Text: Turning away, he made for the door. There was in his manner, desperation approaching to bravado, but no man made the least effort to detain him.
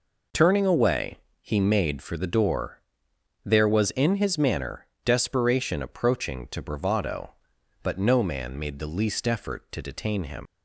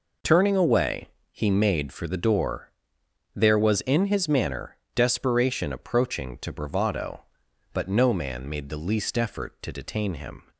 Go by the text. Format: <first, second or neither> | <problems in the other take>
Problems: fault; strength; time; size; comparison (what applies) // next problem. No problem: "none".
second | leaves "him" unfinished; at 10.4 s; 145 ms